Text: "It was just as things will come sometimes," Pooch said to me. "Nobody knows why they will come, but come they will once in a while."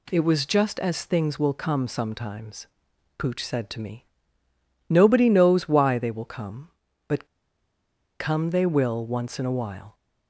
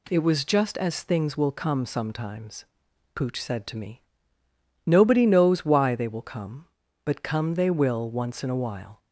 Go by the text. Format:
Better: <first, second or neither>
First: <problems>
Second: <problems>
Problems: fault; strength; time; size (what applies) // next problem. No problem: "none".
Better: second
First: pauses between "but" and "come"; noticeable; at 7.2 s; 0.94 s long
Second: none